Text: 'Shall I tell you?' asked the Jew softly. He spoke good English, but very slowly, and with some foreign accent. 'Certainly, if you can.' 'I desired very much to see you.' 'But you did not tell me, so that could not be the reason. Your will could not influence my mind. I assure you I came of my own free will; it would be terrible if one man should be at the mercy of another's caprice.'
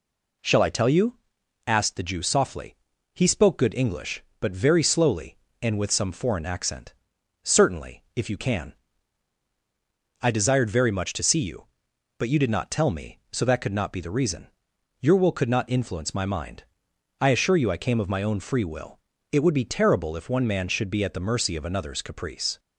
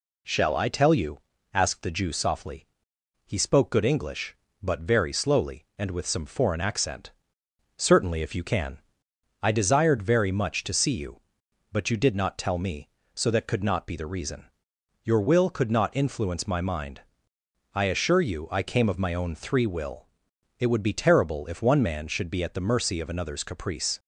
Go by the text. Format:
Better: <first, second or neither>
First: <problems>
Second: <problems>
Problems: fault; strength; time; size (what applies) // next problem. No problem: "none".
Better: first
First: none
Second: says "three" for "free"; at 19.3 s